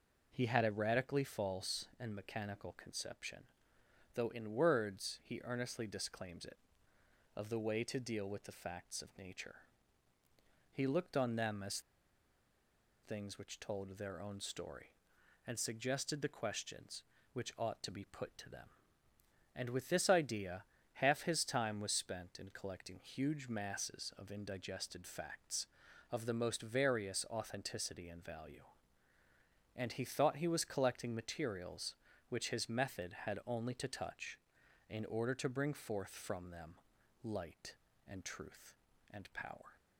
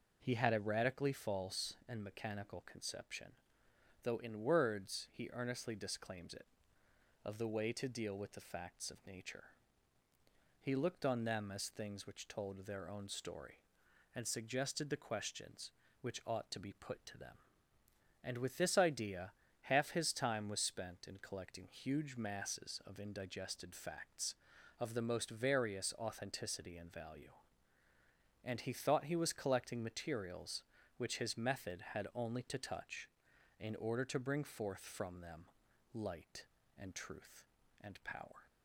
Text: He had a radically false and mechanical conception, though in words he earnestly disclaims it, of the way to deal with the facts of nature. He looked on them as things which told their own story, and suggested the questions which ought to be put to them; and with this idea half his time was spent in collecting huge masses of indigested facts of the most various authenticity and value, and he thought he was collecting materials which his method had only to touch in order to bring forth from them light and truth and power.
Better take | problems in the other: second | pauses between "as" and "things"; at 11.8 s; 1.2 s long // pauses between "idea" and "half"; slight; at 20.6 s; 0.32 s long; slight in the second // pauses between "them" and "light"; noticeable; at 36.7 s; 0.48 s long; noticeable in the second

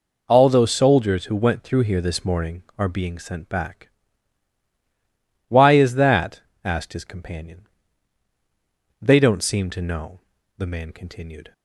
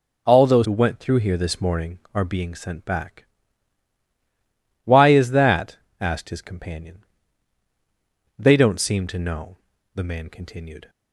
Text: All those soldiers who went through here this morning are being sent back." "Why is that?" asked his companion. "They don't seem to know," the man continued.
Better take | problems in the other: first | skips "soldiers"; at 0.6 s

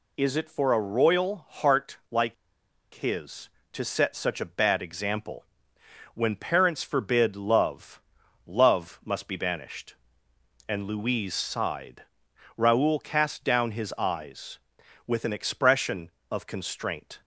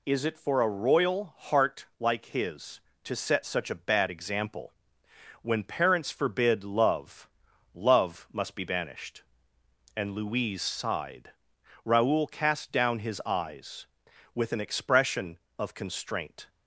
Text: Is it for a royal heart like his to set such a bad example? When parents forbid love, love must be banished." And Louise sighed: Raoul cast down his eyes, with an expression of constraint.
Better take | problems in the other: second | pauses between "like" and "his"; noticeable; at 2.3 s; 0.60 s long

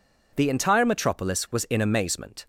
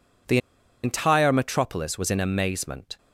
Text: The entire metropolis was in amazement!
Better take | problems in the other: first | pauses between "The" and "entire"; at 0.3 s; 0.45 s long

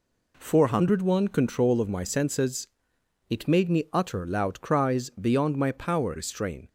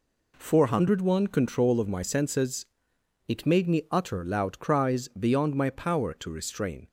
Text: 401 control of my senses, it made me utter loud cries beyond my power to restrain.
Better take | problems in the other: second | skips "to"; at 6.1 s

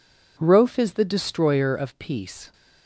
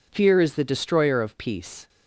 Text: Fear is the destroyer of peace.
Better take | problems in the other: second | says "Rofe" for "Fear"; at 0.4 s

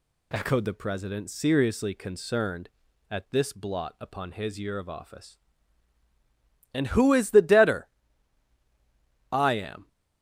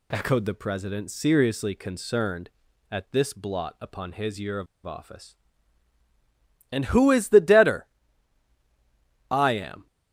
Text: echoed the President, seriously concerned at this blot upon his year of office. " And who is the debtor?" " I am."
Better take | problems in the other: first | pauses between "of" and "office"; slight; at 4.6 s; 0.20 s long

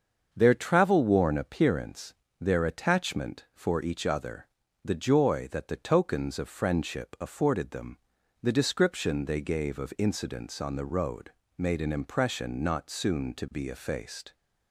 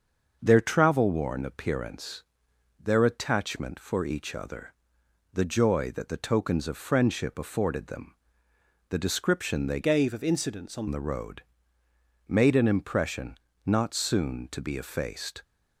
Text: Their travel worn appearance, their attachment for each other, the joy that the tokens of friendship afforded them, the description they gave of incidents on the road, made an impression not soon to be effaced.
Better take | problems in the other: first | starts louder than the rest; until 1.4 s; 6.5 dB; also in the first // changes voice from "gave" to "on"; from 9.8 to 10.8 s; 1.0 s long // pauses between "impression" and "not"; slight; at 13.3 s; 0.26 s long

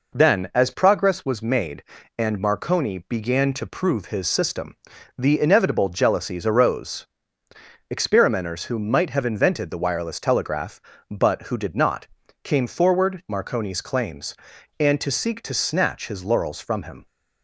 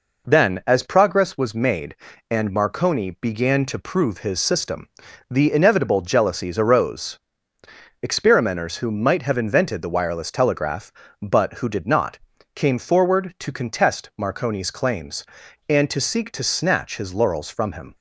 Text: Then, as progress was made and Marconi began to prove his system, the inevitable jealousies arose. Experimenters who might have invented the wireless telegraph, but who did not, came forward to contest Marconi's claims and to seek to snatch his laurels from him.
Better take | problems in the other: second | skips "to contest"; at 13.2 s

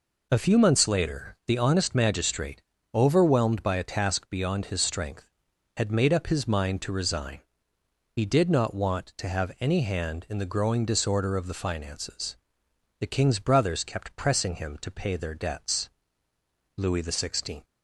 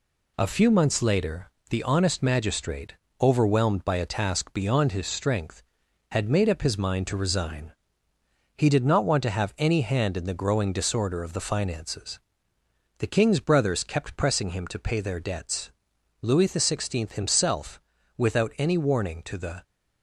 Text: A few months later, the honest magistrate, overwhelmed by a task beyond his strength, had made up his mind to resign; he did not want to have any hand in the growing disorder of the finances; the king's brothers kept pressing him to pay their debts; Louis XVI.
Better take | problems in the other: first | goes on to say "himself without any warning to the"; strong; from 17.1 s on; 2.5 s long

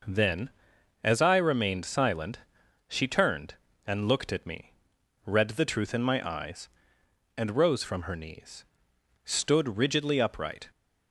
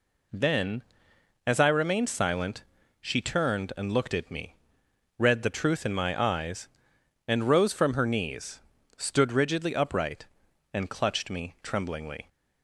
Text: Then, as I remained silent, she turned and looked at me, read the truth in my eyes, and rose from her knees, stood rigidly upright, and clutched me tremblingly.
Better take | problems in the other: second | stops before "and clutched me tremblingly"; at 10.7 s

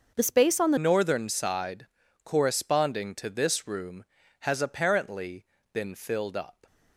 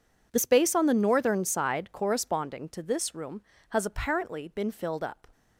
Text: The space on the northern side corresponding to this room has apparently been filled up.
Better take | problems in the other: second | starts louder than the rest; until 1.1 s; 6.5 dB // changes voice at "northern"; from 0.7 s on; 5.9 s long // pauses between "side" and "corresponding"; at 1.8 s; 0.38 s long // pauses between "apparently" and "been"; slight; at 5.4 s; 0.26 s long

